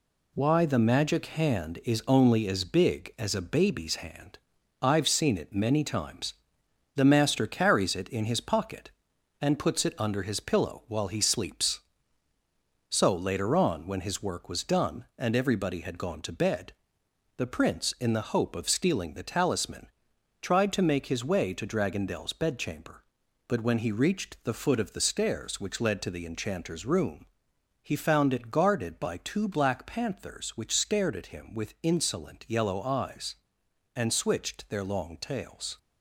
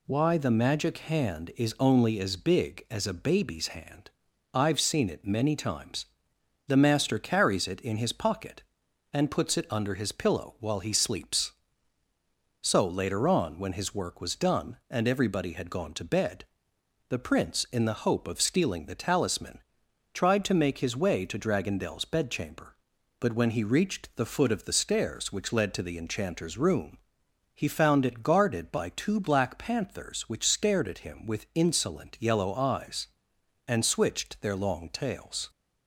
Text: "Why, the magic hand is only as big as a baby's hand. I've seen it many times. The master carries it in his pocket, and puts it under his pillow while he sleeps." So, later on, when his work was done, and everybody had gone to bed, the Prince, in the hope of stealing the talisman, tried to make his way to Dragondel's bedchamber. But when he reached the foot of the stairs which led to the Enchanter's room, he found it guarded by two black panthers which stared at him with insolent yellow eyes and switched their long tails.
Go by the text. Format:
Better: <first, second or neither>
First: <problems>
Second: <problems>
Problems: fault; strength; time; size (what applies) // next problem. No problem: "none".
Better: second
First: gets quieter; noticeable; throughout; 5.5 dB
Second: none